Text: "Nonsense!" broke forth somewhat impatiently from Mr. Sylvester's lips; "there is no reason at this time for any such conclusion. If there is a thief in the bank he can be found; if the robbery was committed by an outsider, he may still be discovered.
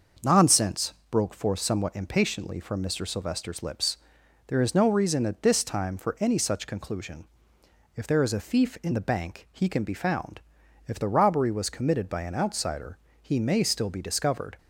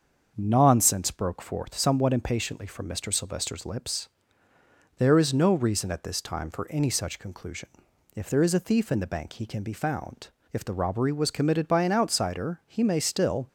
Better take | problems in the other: first | starts louder than the rest; until 1.3 s; 6.5 dB; also in the first // stops before "be discovered"; at 13.4 s

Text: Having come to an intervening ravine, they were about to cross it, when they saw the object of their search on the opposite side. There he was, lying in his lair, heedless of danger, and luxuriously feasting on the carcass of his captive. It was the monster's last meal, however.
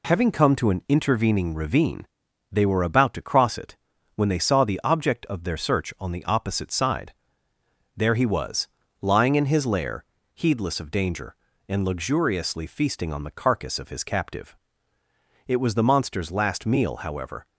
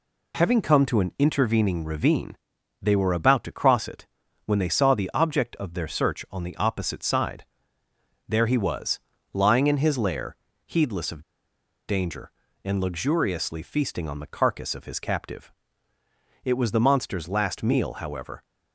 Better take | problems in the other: first | pauses between "of" and "danger"; noticeable; at 11.2 s; 0.65 s long

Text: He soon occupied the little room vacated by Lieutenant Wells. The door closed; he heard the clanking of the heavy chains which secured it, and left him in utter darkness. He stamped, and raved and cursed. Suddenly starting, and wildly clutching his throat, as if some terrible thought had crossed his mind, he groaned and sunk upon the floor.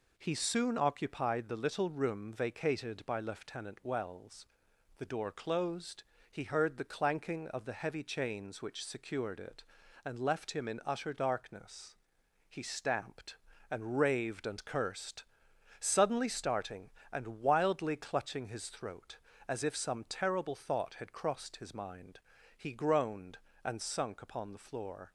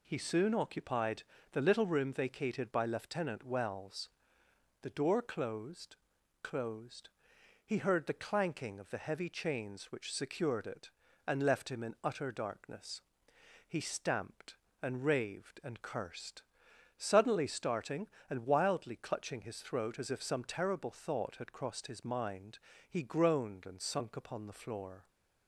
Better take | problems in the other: first | pauses between "occupied" and "the"; slight; at 1.2 s; 0.28 s long // says "closed" twice; at 6.4 s

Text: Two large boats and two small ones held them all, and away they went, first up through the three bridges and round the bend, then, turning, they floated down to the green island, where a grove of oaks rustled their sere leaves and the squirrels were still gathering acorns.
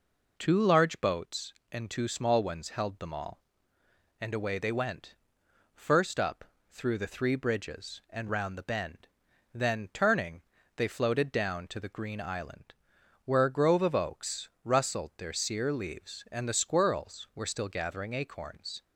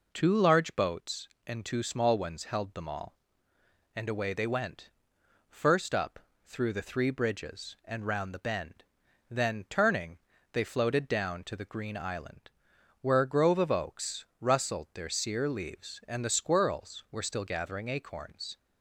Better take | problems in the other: neither | pauses between "up" and "through"; slight; the same in both // pauses between "oaks" and "rustled"; slight; the same in both

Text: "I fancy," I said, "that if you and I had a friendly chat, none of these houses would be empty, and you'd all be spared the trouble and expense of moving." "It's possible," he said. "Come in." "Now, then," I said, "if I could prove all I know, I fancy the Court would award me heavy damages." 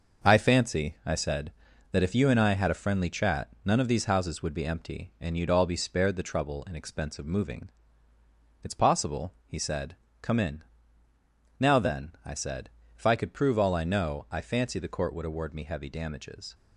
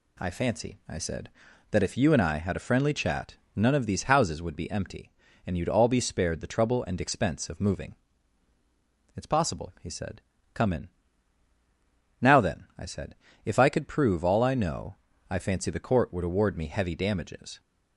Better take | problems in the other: second | gets quieter; throughout; 7 dB

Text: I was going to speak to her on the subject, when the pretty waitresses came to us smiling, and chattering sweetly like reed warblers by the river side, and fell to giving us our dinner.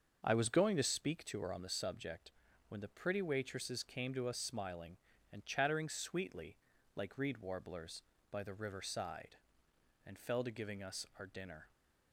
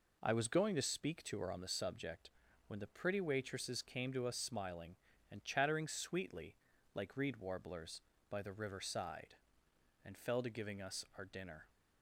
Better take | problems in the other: second | starts louder than the rest; until 1.2 s; 6.5 dB // pauses between "sweetly" and "like"; at 6.5 s; 0.38 s long; also in the second

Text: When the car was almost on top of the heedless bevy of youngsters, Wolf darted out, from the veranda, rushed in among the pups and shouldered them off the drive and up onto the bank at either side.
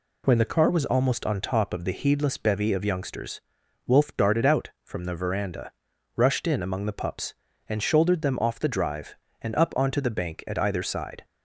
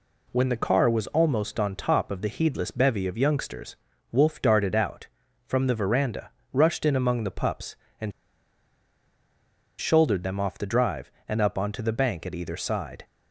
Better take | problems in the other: first | pauses between "and" and "shouldered"; strong; at 8.1 s; 1.6 s long

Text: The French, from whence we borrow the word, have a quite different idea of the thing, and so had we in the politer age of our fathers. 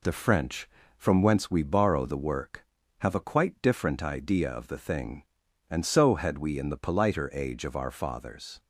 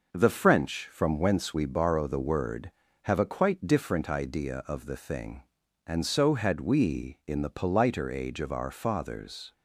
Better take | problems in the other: second | says "work" for "word"; at 2.1 s

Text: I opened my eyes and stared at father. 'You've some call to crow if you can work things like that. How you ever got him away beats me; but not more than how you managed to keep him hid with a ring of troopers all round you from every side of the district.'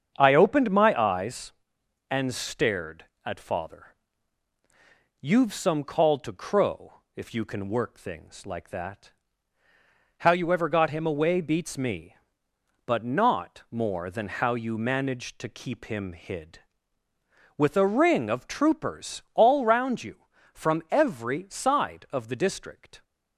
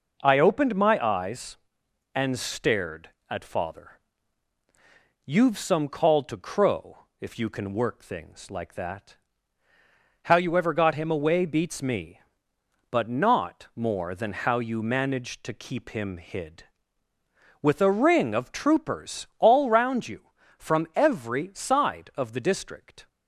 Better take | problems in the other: second | starts louder than the rest; strong; until 1.5 s; 7 dB

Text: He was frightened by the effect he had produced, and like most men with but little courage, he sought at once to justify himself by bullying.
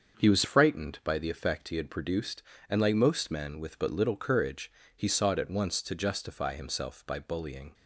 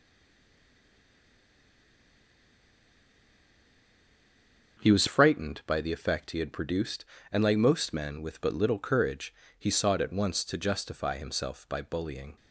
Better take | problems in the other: first | stays silent before the first word; strong; until 4.7 s; 4.7 s long // starts louder than the rest; until 5.8 s; 6.5 dB; also in the first

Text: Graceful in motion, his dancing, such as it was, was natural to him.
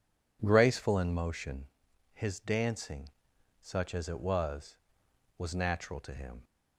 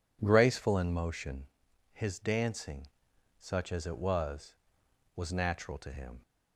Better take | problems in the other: neither | none

